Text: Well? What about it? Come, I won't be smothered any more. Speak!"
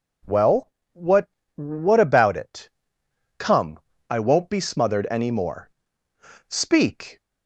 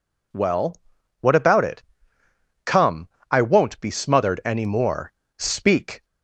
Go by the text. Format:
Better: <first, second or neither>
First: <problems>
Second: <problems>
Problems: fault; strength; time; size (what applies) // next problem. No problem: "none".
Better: second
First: says "What" twice; at 1.5 s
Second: none